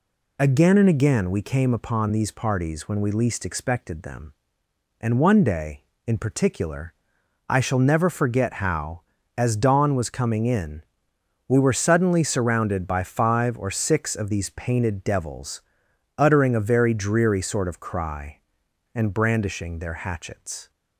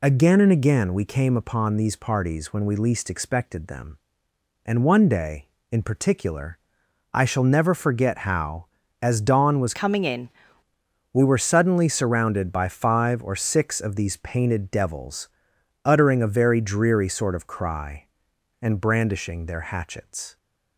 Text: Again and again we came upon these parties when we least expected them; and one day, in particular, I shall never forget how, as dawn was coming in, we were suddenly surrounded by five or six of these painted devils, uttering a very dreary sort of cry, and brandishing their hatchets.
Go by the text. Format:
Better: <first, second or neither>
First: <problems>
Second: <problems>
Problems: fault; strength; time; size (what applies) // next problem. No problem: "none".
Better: first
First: none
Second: changes voice from "coming" to "in"; from 9.7 to 10.2 s; 0.5 s long